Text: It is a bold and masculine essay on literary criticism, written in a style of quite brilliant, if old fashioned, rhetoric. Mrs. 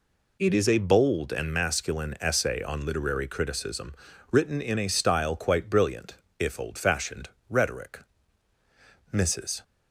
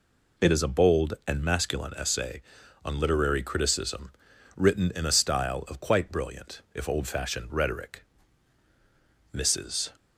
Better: second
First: skips "of"; at 5.3 s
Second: none

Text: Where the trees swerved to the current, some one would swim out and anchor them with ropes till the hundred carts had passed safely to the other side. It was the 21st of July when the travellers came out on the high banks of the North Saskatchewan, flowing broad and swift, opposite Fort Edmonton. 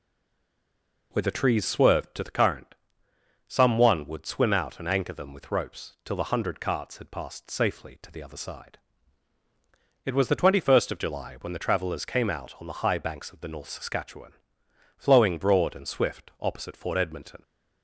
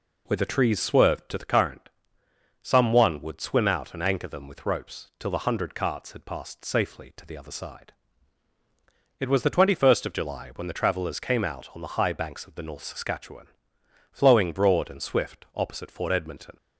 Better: second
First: stays silent before the first word; until 1.1 s; 1.1 s long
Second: none

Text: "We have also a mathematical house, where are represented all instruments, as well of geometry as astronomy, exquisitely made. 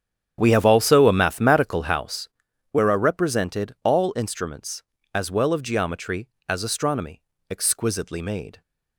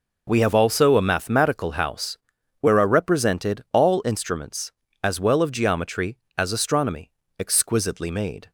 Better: second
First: starts louder than the rest; strong; until 2.2 s; 8.5 dB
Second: none

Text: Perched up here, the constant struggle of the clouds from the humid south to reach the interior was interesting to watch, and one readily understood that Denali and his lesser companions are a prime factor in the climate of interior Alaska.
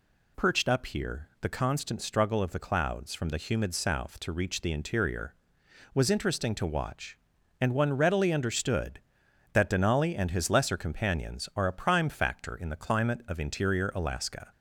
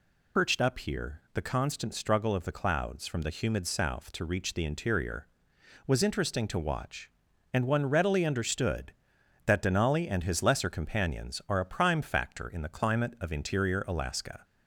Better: first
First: none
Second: loses the start of "Perched"; at 0.3 s; 75 ms

